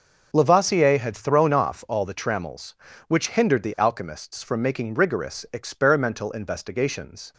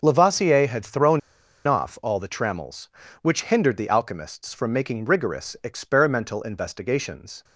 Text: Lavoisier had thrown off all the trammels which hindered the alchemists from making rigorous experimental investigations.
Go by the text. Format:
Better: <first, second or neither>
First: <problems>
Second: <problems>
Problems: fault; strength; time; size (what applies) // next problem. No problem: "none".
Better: first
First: none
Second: pauses between "thrown" and "off"; noticeable; at 1.1 s; 0.47 s long